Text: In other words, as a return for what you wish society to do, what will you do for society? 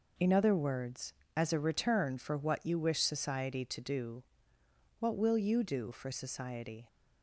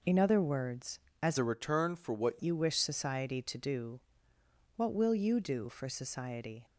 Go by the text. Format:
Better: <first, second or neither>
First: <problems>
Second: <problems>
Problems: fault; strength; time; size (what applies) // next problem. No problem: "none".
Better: first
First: none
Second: changes voice from "a" to "what"; from 1.3 to 2.4 s; 1.1 s long